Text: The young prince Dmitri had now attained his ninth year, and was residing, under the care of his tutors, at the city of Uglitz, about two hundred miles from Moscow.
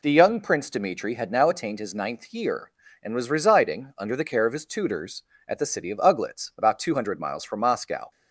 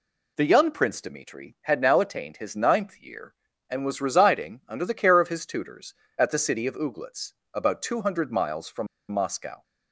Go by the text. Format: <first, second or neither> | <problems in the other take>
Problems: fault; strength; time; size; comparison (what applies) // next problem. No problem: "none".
first | pauses between "from" and "Moscow"; slight; at 8.8 s; 0.24 s long